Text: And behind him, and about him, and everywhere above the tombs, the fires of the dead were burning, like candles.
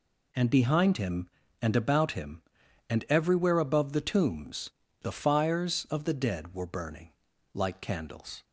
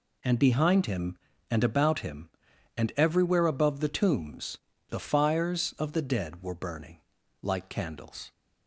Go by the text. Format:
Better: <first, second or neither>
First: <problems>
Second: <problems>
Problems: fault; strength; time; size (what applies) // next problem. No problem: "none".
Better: neither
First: none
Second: none